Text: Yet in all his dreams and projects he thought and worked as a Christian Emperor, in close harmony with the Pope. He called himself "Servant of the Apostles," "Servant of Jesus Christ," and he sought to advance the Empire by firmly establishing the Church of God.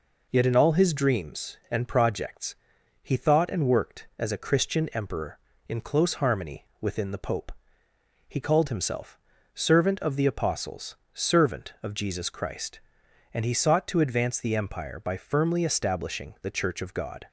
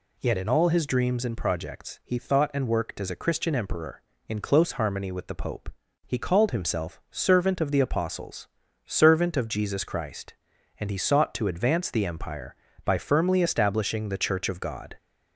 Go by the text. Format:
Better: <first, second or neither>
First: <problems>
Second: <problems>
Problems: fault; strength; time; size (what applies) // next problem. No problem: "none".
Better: second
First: pauses between "projects" and "he"; noticeable; at 2.5 s; 0.46 s long // says "within" for "with"; at 6.8 s // pauses between "himself" and "Servant"; slight; at 9.1 s; 0.36 s long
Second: none